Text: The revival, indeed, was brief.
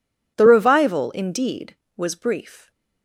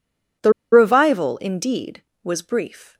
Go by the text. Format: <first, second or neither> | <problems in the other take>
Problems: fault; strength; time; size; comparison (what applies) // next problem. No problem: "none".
first | pauses between "The" and "revival"; slight; at 0.5 s; 0.21 s long